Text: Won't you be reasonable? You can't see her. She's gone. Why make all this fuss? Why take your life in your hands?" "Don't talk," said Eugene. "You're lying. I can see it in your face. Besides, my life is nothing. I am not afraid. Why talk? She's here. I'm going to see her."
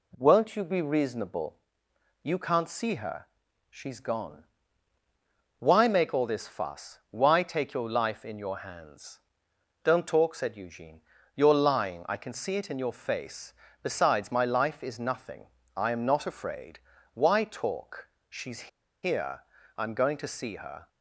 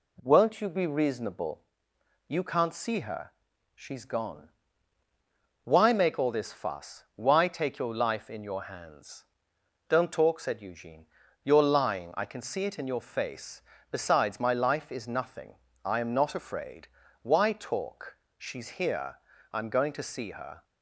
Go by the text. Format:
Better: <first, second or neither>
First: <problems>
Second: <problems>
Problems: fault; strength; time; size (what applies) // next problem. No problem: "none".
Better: second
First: pauses between "She's" and "here"; at 18.6 s; 0.36 s long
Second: none